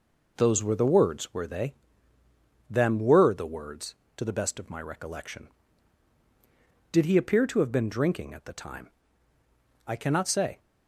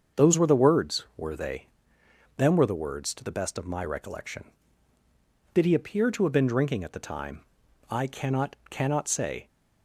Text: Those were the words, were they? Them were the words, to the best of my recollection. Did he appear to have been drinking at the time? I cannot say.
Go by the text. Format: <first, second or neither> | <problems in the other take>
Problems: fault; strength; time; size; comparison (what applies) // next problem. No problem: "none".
first | starts louder than the rest; until 1.2 s; 6.5 dB // says "cannot" twice; at 8.6 s